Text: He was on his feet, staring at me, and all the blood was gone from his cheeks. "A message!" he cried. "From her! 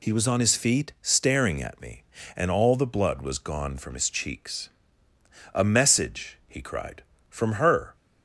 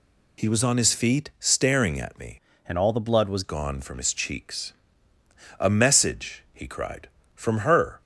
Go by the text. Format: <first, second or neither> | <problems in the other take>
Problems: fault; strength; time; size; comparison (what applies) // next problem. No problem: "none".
first | changes voice from "and" to "was"; from 2.6 to 3.4 s; 0.8 s long